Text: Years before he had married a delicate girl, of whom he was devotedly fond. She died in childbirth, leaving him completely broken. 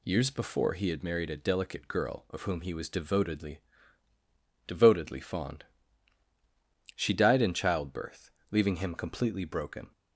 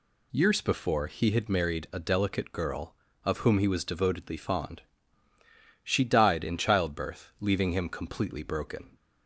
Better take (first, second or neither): second